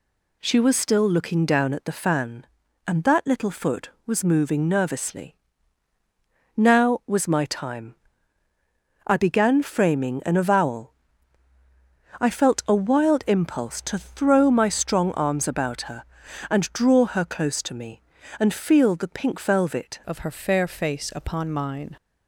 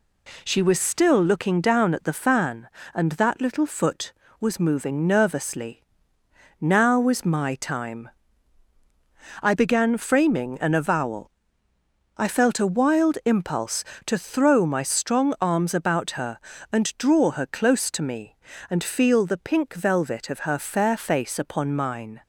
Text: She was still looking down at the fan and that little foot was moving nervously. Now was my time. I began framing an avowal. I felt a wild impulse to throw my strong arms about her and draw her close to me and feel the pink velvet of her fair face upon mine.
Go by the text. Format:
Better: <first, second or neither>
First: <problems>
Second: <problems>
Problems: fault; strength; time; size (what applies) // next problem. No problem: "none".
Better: second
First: changes voice at "of"; from 20.0 s on; 1.9 s long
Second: none